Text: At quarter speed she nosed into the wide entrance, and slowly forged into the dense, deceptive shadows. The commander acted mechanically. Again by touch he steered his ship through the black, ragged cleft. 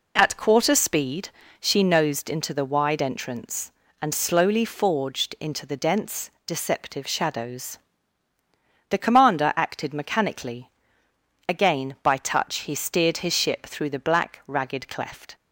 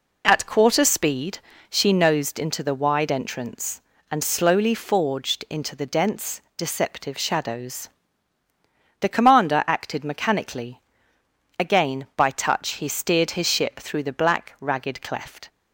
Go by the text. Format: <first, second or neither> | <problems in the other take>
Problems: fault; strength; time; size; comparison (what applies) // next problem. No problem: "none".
neither | pauses between "speed" and "she"; slight; the same in both